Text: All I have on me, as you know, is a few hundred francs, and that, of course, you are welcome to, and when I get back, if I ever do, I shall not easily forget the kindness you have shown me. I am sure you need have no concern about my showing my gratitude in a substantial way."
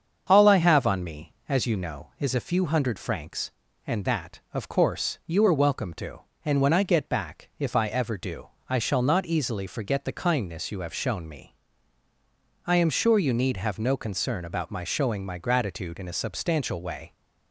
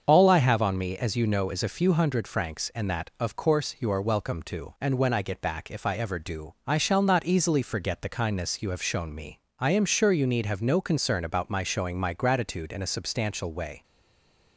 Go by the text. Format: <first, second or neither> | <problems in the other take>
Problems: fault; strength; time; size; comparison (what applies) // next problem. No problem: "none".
first | starts louder than the rest; until 1.0 s; 7 dB; also in the first // stays silent after the last word; slight; from 13.8 s on; 0.7 s long